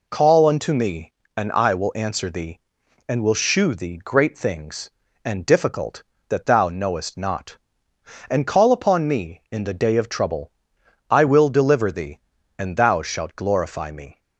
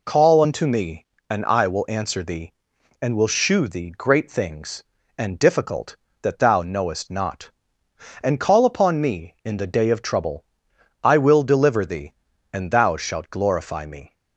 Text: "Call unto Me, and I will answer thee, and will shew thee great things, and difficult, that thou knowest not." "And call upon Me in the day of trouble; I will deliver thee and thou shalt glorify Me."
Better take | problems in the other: neither | none

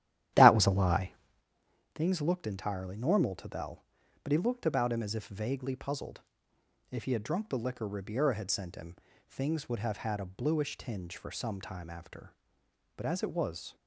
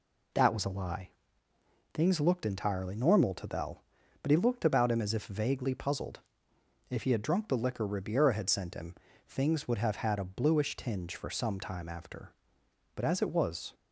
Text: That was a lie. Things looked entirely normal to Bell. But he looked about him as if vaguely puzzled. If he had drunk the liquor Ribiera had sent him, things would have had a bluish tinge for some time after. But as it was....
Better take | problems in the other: second | starts louder than the rest; strong; until 1.5 s; 12 dB

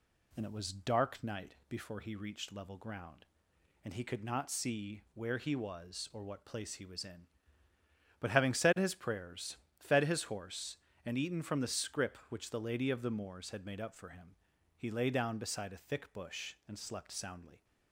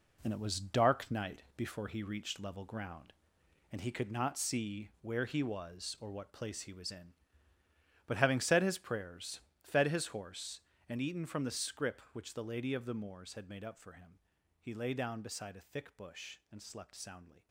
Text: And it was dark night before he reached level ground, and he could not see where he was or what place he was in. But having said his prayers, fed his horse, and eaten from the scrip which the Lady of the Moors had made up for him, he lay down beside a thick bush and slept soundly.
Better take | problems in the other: first | gets quieter; strong; throughout; 9 dB

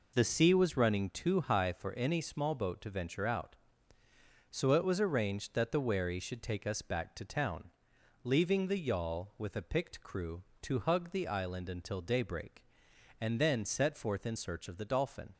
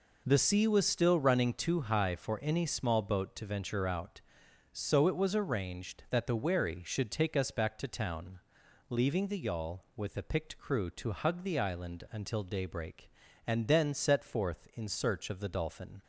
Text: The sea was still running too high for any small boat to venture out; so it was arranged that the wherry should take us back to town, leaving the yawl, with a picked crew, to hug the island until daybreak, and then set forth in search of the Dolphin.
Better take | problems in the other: second | skips "still"; at 0.7 s

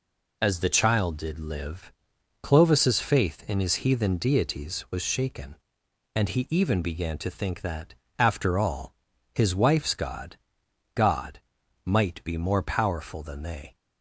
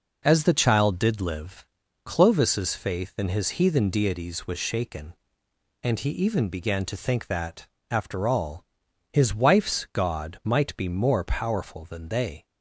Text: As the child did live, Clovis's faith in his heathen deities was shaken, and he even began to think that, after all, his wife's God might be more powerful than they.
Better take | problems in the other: second | says "God" twice; at 10.9 s

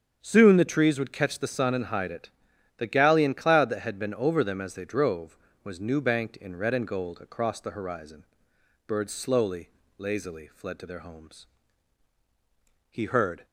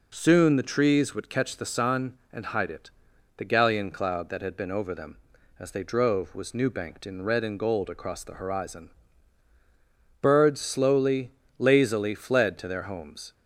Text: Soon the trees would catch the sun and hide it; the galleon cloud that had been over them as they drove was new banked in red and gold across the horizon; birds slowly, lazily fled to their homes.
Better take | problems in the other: second | starts louder than the rest; strong; until 1.2 s; 7.5 dB // goes on to say "He heard"; from 12.9 s on; 0.54 s long

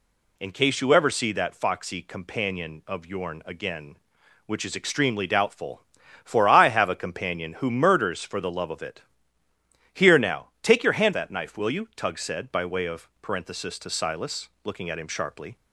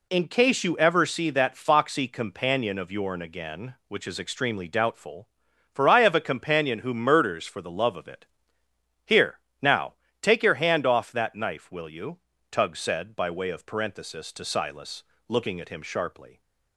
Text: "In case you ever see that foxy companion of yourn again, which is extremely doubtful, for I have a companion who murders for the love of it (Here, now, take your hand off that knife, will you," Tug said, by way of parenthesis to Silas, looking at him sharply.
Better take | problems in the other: second | skips "off"; at 11.1 s

